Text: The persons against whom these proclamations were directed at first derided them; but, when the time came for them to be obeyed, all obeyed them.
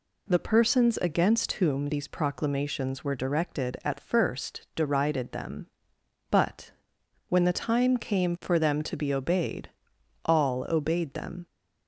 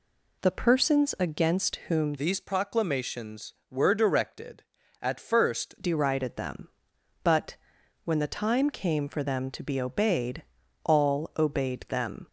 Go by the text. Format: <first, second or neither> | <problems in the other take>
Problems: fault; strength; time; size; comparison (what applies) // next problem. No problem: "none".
first | changes voice from "these" to "first"; from 2.1 to 5.7 s; 3.6 s long